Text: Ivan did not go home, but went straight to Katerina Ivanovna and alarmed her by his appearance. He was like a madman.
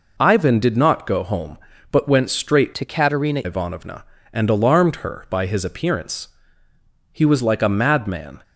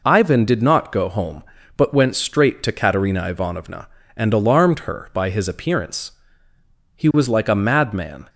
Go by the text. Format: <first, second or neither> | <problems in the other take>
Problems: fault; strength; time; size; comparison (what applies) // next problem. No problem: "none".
second | changes voice from "to" to "Katerina"; from 2.7 to 3.4 s; 0.7 s long